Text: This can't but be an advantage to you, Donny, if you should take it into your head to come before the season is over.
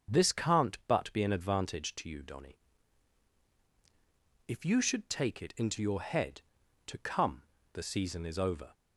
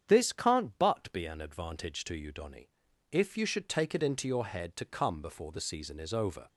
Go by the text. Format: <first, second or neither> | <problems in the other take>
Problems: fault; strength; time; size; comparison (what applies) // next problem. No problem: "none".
second | starts louder than the rest; strong; until 1.2 s; 7 dB; strong in the second // skips "before"; at 7.5 s